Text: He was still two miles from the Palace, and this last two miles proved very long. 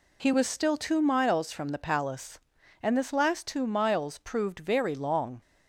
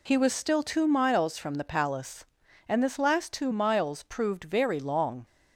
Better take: neither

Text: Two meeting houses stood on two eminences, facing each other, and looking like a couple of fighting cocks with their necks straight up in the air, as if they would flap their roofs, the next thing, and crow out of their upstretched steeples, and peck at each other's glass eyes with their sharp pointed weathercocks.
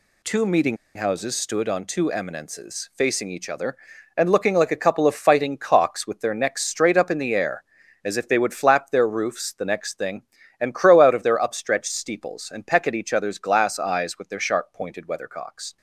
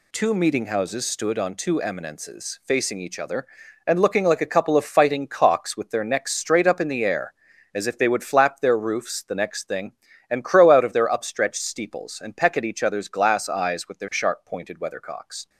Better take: second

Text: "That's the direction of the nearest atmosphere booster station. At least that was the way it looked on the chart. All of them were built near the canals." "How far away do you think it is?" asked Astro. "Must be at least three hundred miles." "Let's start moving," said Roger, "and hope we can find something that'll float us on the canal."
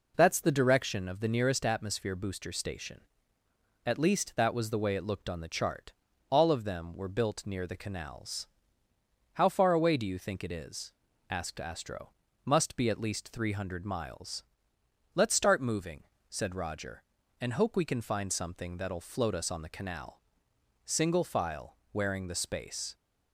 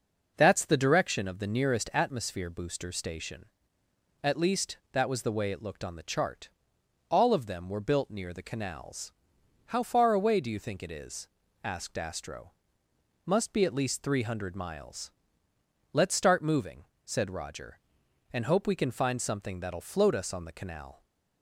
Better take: second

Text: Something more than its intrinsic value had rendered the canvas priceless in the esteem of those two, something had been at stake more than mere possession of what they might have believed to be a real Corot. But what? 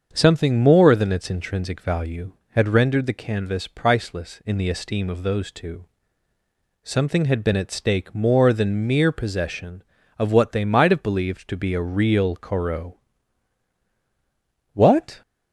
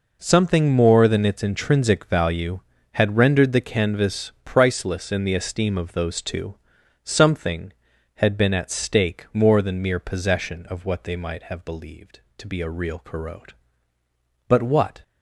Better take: second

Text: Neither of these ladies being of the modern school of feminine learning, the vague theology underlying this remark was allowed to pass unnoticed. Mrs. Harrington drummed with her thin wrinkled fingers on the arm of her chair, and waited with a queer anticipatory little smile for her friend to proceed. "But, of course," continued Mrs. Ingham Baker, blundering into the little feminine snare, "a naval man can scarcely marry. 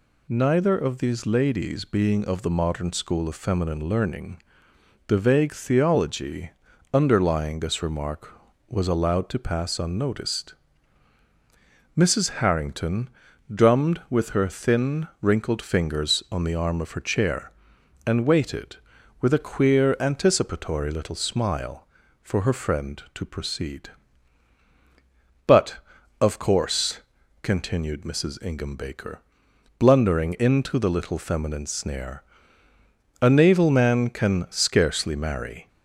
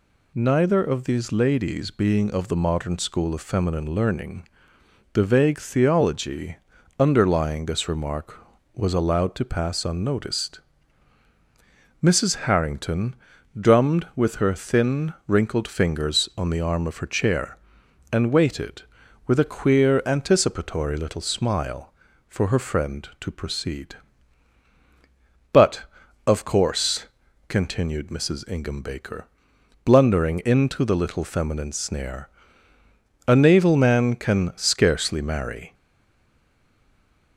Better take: first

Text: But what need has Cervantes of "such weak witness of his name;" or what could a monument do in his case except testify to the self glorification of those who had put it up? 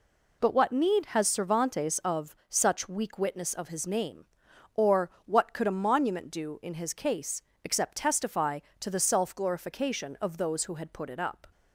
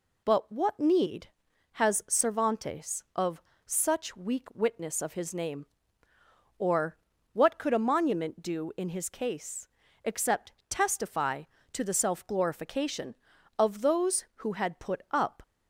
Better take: first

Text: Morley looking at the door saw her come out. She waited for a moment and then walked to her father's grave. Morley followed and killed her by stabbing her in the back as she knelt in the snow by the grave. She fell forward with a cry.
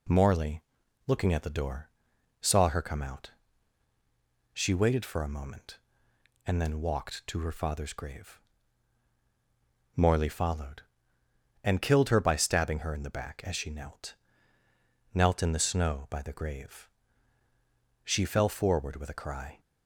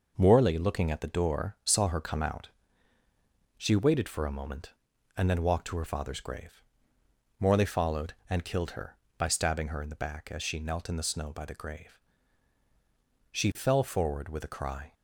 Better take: second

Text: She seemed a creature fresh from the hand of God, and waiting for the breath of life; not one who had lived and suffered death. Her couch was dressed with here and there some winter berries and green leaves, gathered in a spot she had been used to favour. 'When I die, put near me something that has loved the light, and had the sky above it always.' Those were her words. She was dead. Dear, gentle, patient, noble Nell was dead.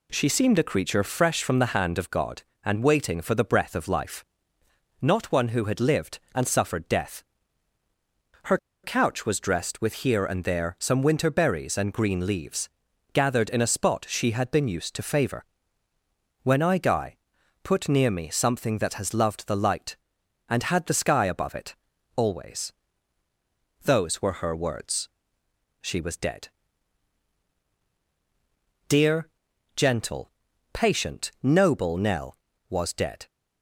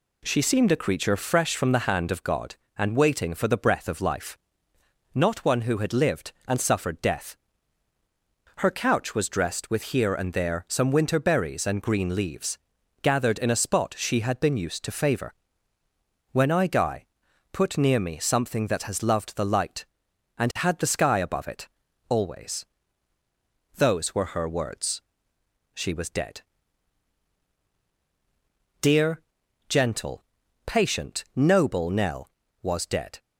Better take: second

